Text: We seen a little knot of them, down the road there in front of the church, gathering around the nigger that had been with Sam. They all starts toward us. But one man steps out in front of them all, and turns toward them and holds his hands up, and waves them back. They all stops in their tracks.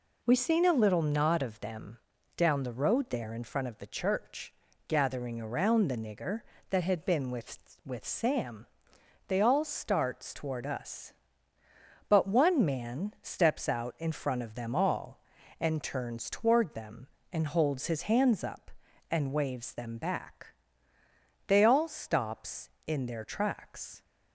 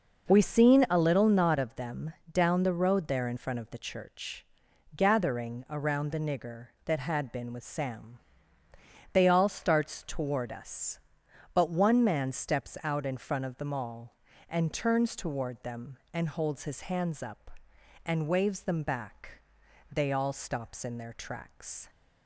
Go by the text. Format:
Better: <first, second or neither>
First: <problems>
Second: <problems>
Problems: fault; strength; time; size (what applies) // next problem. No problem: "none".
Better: second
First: says "with" twice; at 7.8 s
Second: none